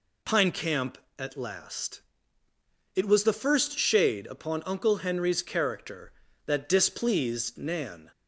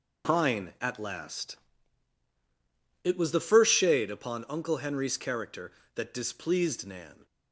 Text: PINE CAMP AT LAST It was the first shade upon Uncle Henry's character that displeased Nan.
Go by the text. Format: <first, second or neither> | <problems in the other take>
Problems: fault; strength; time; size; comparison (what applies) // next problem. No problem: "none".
first | skips "CAMP"; at 0.7 s // pauses between "LAST" and "It"; strong; at 1.5 s; 1.4 s long; noticeable in the first